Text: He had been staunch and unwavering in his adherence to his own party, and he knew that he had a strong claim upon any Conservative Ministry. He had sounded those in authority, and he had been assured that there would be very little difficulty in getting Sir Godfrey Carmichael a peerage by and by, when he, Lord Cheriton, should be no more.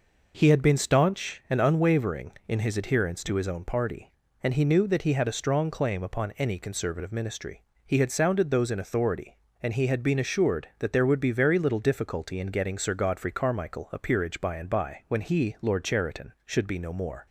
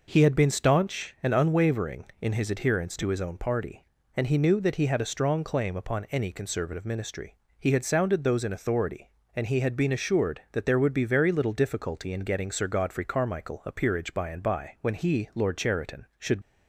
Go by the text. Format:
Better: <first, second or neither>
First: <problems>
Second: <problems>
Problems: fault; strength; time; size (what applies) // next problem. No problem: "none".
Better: first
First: none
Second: stops before "be no more"; at 16.4 s